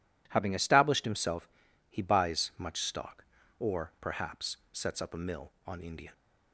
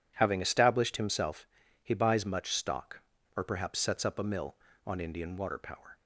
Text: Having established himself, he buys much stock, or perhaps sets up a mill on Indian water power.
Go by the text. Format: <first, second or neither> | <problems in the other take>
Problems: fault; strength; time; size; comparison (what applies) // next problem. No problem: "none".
second | pauses between "perhaps" and "sets"; slight; at 4.5 s; 0.16 s long // stops before "water power"; at 6.1 s